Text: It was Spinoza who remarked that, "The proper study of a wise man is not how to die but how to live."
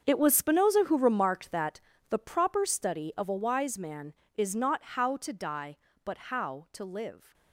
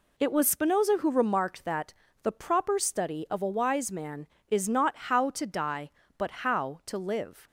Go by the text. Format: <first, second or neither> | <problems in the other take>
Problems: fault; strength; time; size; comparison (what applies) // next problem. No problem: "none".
second | gets quieter; strong; throughout; 14.5 dB // pauses between "not" and "how"; slight; at 4.8 s; 0.16 s long; slight in the second